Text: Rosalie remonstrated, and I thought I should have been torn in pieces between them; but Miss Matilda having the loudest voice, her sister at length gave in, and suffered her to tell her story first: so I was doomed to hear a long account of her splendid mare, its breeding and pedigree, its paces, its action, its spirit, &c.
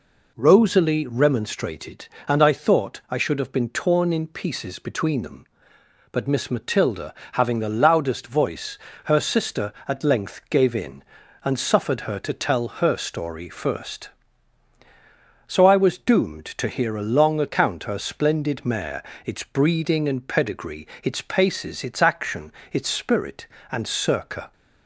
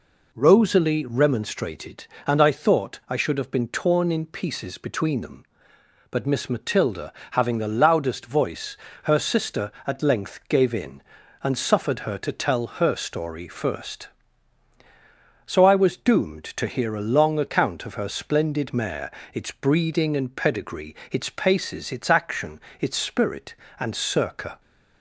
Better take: second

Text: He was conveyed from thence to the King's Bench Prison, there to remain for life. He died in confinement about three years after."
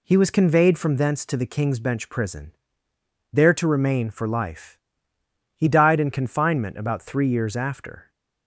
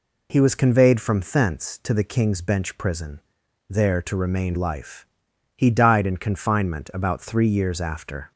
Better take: first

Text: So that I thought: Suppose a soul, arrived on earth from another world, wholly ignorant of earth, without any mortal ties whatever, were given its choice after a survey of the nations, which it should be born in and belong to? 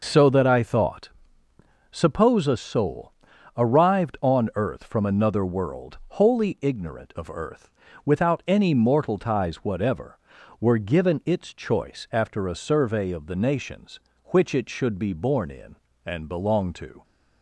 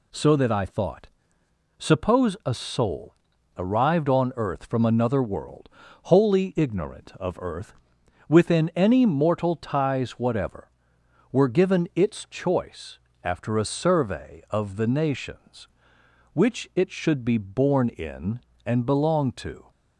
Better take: first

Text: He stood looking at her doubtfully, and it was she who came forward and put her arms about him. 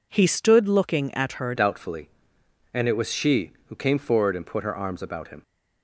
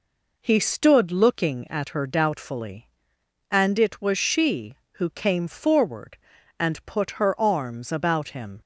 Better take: second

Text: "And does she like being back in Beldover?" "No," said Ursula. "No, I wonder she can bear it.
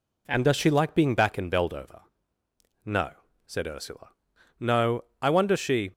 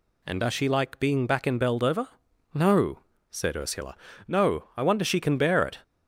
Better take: second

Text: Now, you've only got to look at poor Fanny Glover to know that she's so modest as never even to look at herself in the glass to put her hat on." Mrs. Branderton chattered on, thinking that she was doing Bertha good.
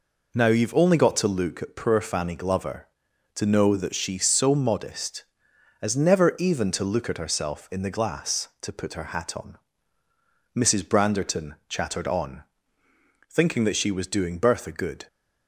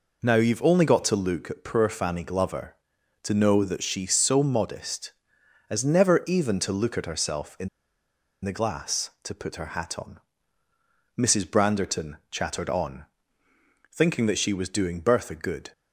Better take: first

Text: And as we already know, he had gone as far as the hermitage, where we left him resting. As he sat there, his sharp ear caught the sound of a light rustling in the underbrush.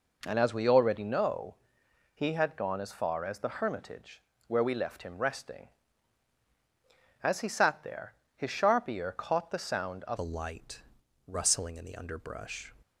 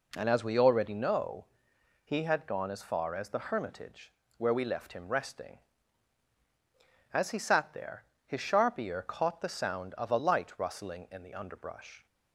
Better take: second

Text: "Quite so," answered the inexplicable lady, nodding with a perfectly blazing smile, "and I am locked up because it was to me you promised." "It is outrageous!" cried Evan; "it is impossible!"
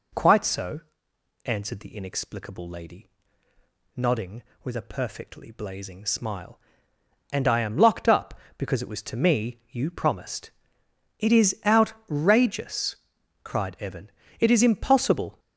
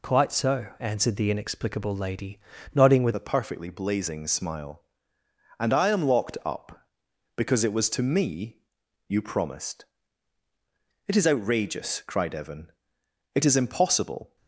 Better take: first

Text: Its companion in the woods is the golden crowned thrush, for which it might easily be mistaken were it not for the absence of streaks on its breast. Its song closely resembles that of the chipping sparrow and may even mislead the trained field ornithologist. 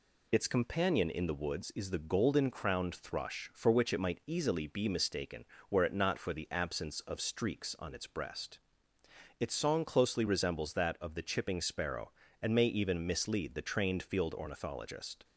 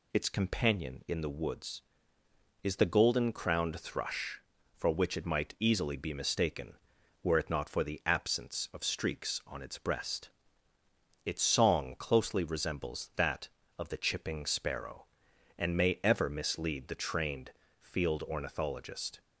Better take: first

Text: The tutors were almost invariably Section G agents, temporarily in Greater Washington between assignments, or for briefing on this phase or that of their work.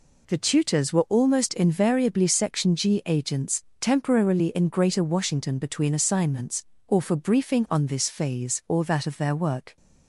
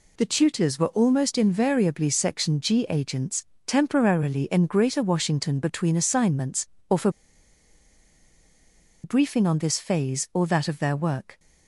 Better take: first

